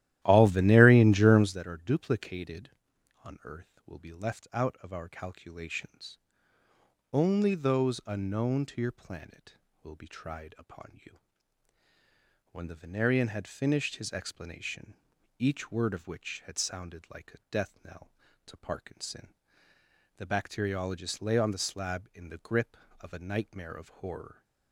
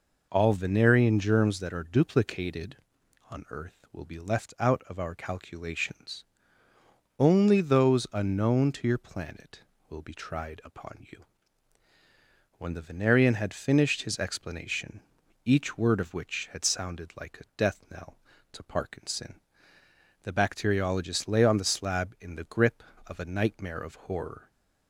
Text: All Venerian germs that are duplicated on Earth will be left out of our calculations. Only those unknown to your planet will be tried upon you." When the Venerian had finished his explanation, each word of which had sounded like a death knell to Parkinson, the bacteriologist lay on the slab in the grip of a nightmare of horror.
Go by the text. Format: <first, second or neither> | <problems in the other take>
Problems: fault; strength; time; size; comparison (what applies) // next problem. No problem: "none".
second | starts louder than the rest; strong; until 1.6 s; 14 dB